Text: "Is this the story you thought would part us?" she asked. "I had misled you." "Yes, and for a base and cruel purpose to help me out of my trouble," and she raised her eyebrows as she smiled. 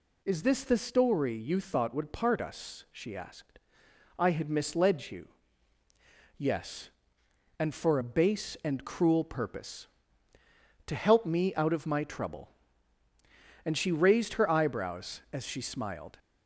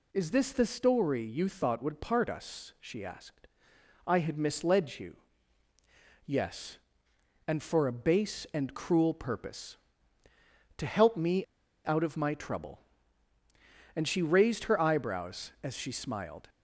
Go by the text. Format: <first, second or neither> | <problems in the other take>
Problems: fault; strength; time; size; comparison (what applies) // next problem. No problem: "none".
first | pauses between "me" and "out"; at 11.4 s; 0.39 s long